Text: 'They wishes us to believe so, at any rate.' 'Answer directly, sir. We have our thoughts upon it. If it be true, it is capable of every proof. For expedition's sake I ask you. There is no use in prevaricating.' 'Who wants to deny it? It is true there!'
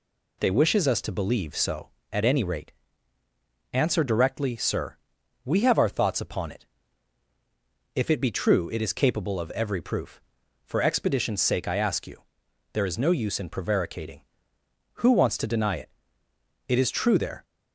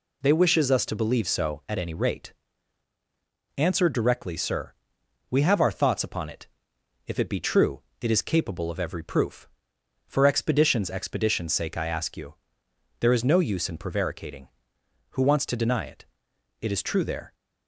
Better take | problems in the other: first | says "expedition's" twice; at 10.8 s

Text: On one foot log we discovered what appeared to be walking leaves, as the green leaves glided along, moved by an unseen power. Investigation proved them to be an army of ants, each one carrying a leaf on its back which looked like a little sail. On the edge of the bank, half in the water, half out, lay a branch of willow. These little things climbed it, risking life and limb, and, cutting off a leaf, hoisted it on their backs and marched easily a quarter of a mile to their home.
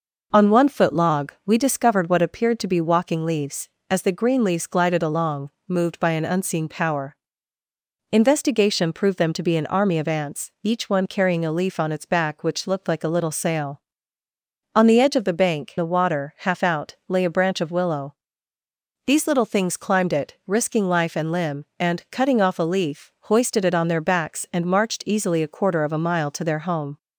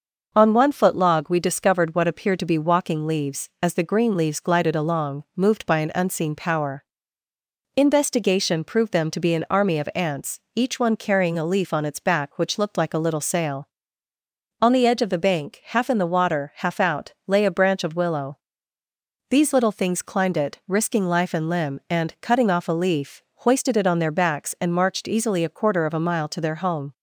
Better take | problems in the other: second | skips "half in"; at 15.7 s

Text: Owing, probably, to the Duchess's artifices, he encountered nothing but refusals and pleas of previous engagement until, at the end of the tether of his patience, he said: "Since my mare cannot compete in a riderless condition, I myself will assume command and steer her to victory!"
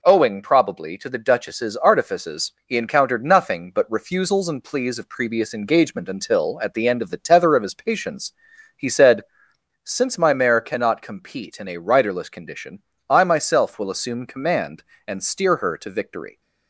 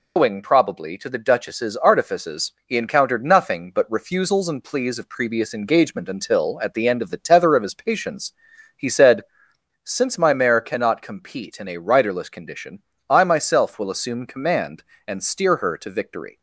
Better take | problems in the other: first | loses the start of "Owing"; at 0.1 s; 125 ms

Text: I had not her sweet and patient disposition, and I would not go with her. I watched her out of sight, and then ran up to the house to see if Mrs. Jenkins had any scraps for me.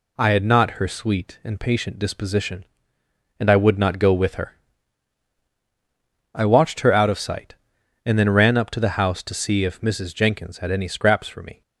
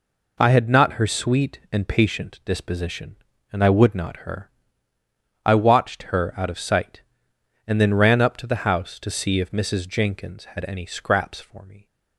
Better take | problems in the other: first | skips "go with"; at 4.1 s

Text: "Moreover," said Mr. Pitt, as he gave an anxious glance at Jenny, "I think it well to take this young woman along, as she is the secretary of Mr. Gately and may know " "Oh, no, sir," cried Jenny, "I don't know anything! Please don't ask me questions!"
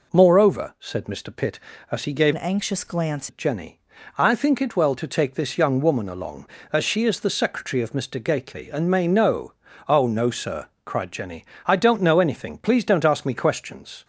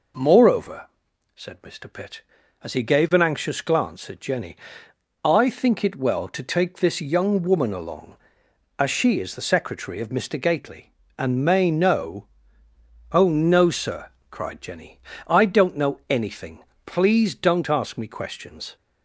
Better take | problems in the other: second | changes voice from "an" to "glance"; from 2.3 to 3.2 s; 0.9 s long

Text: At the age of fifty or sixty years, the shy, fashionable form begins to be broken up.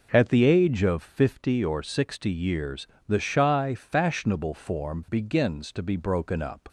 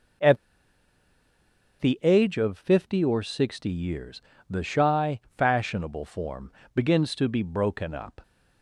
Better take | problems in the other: first | pauses between "At" and "the"; strong; at 0.3 s; 1.4 s long // pauses between "form" and "begins"; slight; at 6.5 s; 0.24 s long

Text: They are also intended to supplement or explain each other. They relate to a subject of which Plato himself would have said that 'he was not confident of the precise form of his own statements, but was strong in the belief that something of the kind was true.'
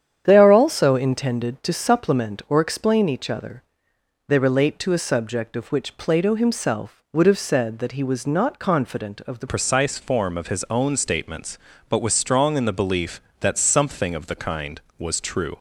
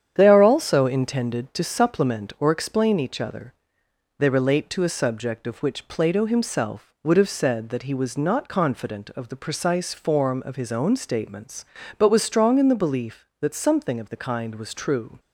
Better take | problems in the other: second | starts louder than the rest; strong; until 1.2 s; 9 dB; strong in the second // changes voice at "precise"; from 9.4 s on; 6.1 s long

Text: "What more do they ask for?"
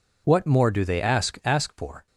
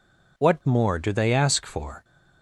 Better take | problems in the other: second | says "ask" twice; at 1.4 s

